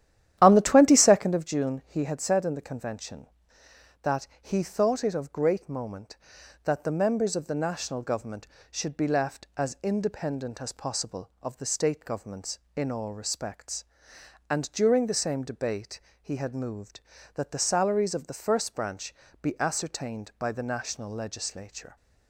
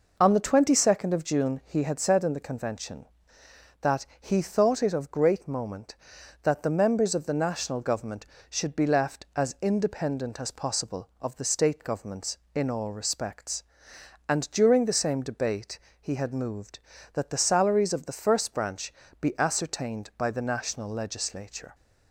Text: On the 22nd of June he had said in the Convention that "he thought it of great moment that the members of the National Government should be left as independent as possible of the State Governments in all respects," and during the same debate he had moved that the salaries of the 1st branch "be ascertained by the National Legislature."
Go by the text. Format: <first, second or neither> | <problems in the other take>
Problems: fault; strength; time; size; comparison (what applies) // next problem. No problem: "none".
second | starts louder than the rest; strong; until 1.4 s; 11.5 dB // pauses between "debate" and "he"; slight; at 15.9 s; 0.22 s long; slight in the second // pauses between "branch" and "be"; slight; at 19.1 s; 0.26 s long; slight in the second